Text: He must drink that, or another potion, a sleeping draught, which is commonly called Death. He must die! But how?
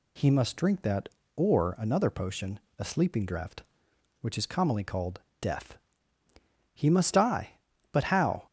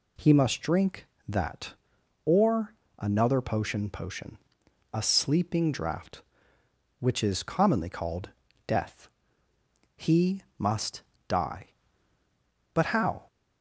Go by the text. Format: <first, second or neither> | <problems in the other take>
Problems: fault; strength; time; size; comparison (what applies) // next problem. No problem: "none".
first | pauses between "or" and "another"; slight; at 2.7 s; 0.26 s long // says "potion" twice; at 3.8 s // pauses between "called" and "Death"; slight; at 8.3 s; 0.34 s long; slight in the first // pauses between "He" and "must"; slight; at 10.4 s; 0.16 s long // pauses between "must" and "die"; slight; at 11.0 s; 0.24 s long